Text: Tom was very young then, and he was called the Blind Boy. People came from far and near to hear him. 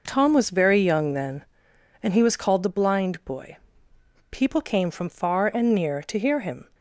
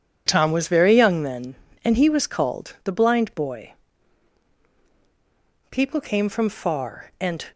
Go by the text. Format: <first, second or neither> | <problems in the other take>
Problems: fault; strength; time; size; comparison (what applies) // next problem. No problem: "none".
first | stops before "near to hear him"; at 7.5 s